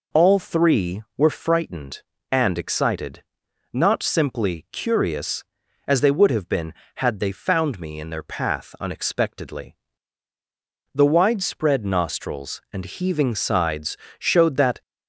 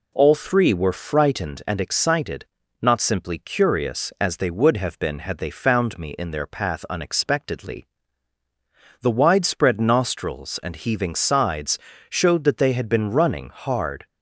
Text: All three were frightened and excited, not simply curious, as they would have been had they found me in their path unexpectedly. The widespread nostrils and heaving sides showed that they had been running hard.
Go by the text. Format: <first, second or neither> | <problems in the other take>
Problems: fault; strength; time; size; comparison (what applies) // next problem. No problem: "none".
second | pauses between "sides" and "showed"; slight; at 13.9 s; 0.24 s long; slight in the second // stops before "they had been running hard"; at 14.8 s